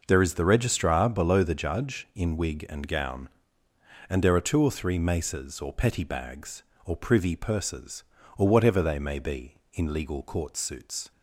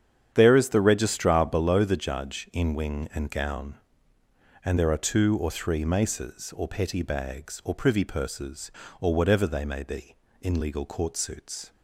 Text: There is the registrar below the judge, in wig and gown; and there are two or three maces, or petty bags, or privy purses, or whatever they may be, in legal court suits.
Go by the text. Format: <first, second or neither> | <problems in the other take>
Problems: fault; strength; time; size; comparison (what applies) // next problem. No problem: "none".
first | starts louder than the rest; strong; until 1.3 s; 8.5 dB // says "wing" for "wig"; at 2.7 s